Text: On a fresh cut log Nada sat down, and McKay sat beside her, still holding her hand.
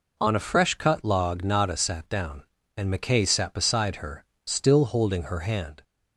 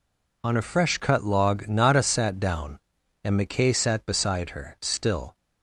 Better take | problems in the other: first | stops before "holding her hand"; at 5.3 s

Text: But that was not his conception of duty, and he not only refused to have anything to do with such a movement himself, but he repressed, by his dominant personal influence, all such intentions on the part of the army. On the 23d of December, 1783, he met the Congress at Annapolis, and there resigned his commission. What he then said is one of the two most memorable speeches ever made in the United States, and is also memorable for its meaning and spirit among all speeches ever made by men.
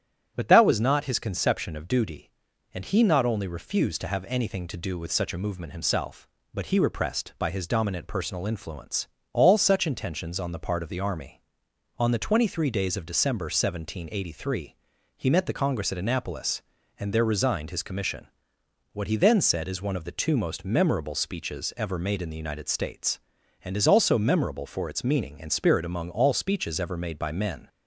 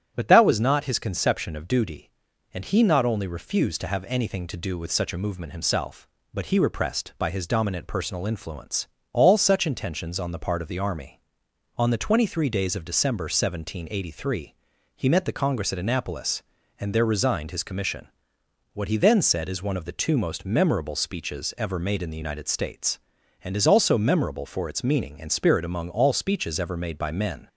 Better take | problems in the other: neither | starts louder than the rest; strong; the same in both

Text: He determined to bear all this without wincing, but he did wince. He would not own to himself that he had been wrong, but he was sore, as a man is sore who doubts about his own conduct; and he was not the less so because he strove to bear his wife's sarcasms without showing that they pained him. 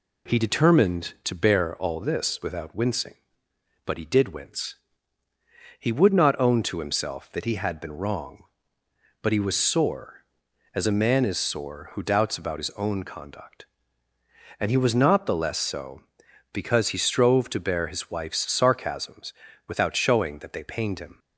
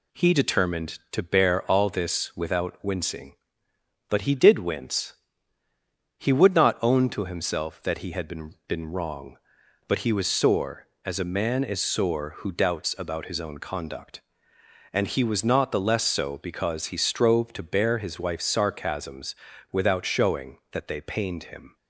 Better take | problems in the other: first | says "been" twice; at 8.6 s // pauses between "sarcasms" and "without"; at 19.3 s; 0.38 s long; slight in the first

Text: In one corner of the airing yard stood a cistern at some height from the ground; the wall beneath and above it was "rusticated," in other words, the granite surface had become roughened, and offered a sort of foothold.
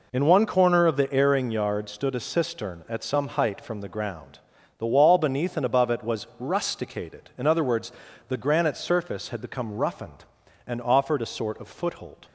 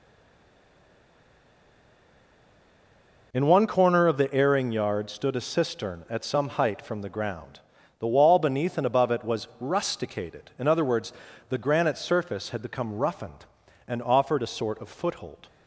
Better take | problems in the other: first | stays silent before the first word; strong; until 3.3 s; 3.3 s long

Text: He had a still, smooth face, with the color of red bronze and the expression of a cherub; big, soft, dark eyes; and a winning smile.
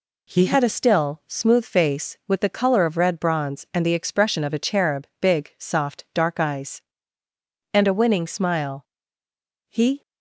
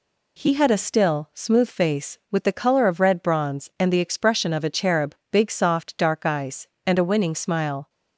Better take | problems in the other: second | goes on to say "He"; slight; from 9.6 s on; 0.32 s long

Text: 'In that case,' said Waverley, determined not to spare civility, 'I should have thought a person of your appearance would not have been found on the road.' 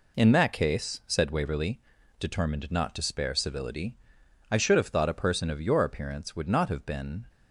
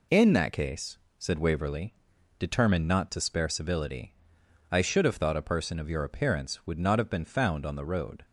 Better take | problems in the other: second | stops before "found on the road"; at 7.2 s

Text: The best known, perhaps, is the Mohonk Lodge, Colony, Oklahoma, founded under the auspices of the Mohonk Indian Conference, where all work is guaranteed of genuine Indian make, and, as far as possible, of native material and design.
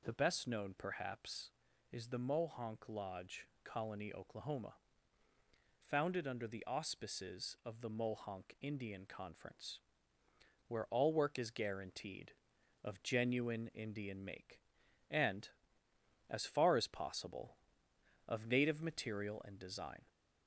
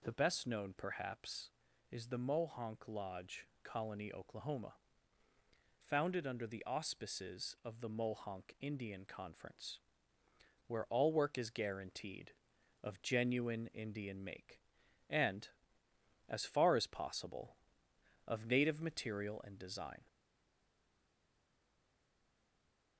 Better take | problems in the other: first | stays silent after the last word; strong; from 20.0 s on; 2.9 s long

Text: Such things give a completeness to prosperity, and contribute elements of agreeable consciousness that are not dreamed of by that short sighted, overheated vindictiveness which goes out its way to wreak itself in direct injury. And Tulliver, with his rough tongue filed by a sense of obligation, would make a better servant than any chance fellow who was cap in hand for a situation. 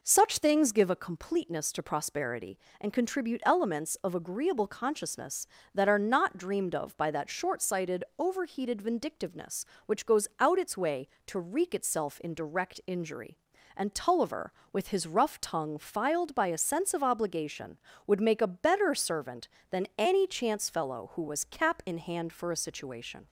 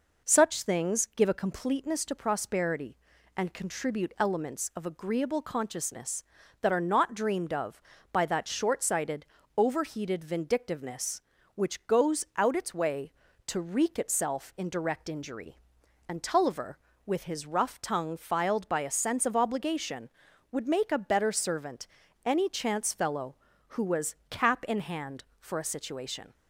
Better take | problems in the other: first | skips "than"; at 22.0 s

